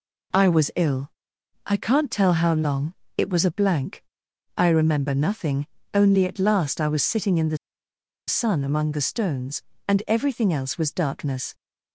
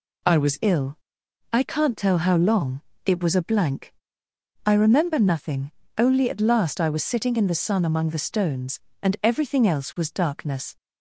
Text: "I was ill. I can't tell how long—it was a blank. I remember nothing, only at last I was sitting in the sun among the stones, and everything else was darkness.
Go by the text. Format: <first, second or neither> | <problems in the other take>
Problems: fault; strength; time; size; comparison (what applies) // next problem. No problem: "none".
second | pauses between "the" and "sun"; noticeable; at 7.5 s; 0.71 s long